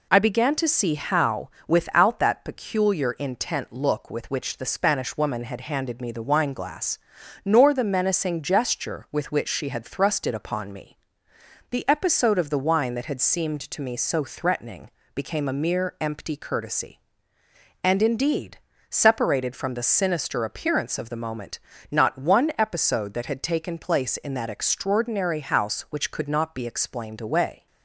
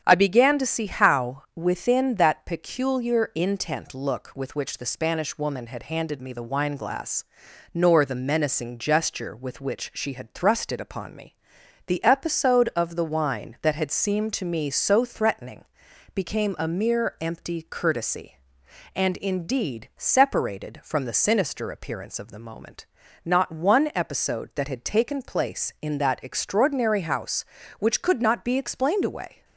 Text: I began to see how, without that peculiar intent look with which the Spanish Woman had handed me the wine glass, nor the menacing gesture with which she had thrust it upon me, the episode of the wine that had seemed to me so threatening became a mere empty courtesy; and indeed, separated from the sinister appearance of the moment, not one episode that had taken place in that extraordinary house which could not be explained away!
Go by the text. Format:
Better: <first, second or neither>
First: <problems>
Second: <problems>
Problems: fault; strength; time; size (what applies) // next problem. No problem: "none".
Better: first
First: pauses between "threatening" and "became"; slight; at 14.8 s; 0.26 s long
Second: starts louder than the rest; strong; until 1.0 s; 8 dB // says "within" for "without"; at 1.5 s // pauses between "threatening" and "became"; noticeable; at 15.6 s; 0.52 s long